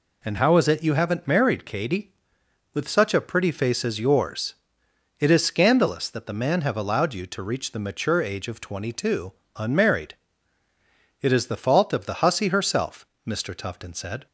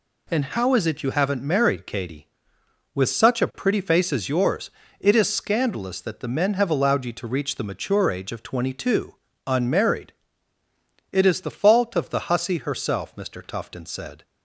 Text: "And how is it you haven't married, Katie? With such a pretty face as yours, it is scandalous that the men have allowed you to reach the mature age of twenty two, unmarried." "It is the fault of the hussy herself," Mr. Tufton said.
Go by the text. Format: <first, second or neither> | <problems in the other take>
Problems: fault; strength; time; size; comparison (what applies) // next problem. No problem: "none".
second | says "man" for "men"; at 6.3 s